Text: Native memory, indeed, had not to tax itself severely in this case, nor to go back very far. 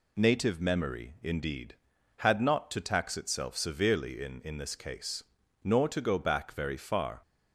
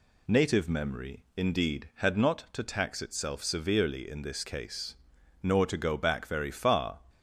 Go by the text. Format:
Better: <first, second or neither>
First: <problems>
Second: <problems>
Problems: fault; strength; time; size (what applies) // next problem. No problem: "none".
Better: second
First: says "in" twice; at 4.4 s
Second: none